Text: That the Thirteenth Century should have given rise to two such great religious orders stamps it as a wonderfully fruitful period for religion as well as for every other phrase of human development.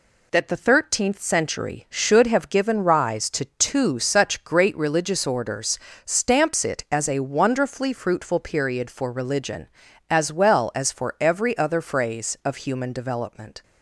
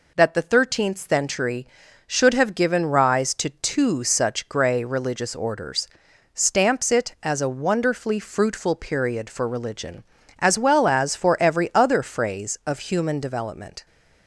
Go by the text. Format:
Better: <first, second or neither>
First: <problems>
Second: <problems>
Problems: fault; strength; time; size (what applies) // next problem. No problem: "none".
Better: first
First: pauses between "orders" and "stamps"; slight; at 5.7 s; 0.28 s long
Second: says "grey" for "great"; at 4.4 s // pauses between "orders" and "stamps"; noticeable; at 5.8 s; 0.48 s long